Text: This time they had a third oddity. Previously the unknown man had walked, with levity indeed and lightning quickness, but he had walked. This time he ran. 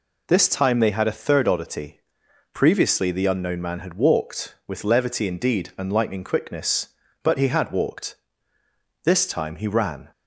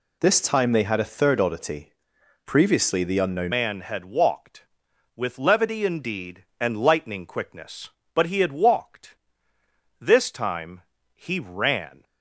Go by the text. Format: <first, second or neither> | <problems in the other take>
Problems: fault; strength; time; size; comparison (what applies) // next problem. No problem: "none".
first | changes voice at "man"; from 3.5 s on; 8.5 s long // pauses between "time" and "he"; slight; at 10.8 s; 0.34 s long